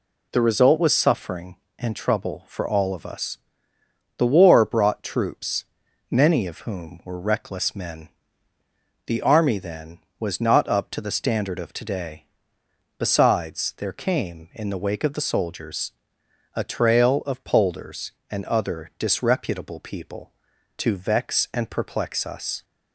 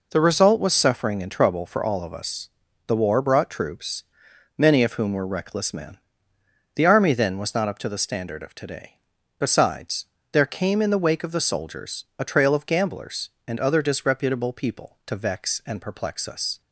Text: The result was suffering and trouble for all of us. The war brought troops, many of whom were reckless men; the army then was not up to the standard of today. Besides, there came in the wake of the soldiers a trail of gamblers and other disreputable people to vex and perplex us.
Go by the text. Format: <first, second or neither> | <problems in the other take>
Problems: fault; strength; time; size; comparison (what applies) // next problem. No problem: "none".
second | pauses between "soldiers" and "a"; noticeable; at 15.9 s; 0.64 s long // says "polders" for "gamblers"; at 17.4 s